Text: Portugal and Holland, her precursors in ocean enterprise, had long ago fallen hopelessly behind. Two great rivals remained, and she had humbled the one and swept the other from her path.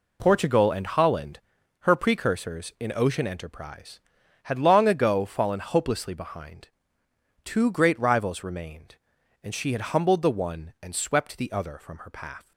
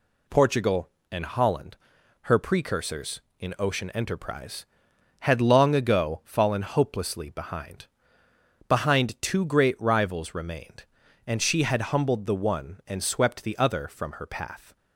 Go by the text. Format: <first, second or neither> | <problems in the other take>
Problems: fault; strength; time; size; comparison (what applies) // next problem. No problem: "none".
first | says "behind" twice; at 8.6 s